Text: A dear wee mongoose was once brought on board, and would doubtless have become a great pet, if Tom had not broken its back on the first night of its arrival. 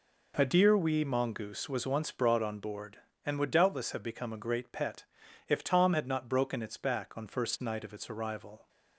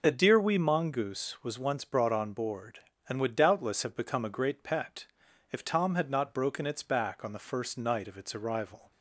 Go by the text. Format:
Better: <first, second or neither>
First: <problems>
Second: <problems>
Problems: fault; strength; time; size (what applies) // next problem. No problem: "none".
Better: second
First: skips "the"; at 7.2 s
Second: none